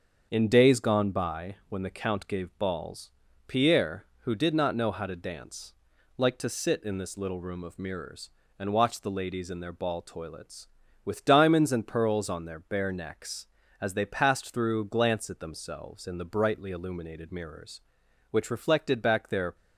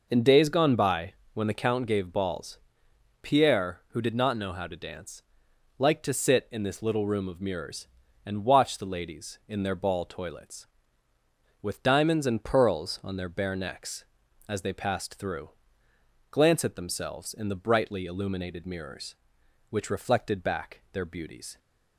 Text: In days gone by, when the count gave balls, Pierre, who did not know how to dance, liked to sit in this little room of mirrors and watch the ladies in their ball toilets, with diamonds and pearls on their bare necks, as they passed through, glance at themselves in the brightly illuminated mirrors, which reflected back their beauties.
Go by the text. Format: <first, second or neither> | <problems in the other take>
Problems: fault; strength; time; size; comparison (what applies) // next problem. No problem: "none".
second | starts louder than the rest; until 1.3 s; 7 dB // stops before "beauties"; at 19.5 s